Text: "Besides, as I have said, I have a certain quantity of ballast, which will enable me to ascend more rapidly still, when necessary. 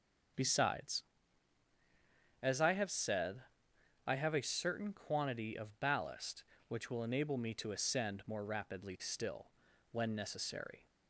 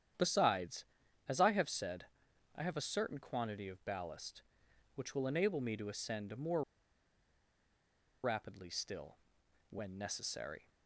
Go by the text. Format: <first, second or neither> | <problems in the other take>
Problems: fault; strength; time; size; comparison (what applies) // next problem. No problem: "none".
first | starts louder than the rest; strong; until 1.6 s; 9.5 dB; also in the first // pauses between "more" and "rapidly"; strong; at 6.6 s; 1.6 s long